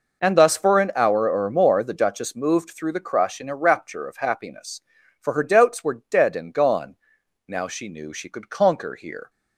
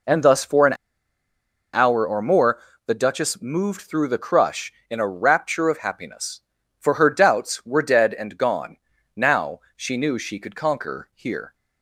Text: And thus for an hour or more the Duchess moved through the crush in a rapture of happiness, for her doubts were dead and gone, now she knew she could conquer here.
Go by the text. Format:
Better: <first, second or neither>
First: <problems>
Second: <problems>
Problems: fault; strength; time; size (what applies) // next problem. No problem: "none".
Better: first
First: none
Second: pauses between "an" and "hour"; at 0.7 s; 0.99 s long // pauses between "more" and "the"; slight; at 2.5 s; 0.28 s long // pauses between "now" and "she"; slight; at 9.6 s; 0.16 s long